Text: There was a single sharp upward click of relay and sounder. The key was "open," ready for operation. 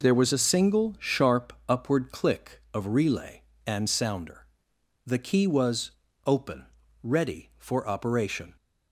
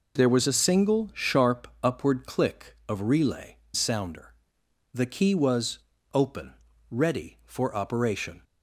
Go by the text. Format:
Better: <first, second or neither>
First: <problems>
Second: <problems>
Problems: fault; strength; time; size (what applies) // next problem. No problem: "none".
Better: first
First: pauses between "was" and "open"; slight; at 5.9 s; 0.34 s long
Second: skips "and"; at 3.6 s // pauses between "was" and "open"; slight; at 5.7 s; 0.34 s long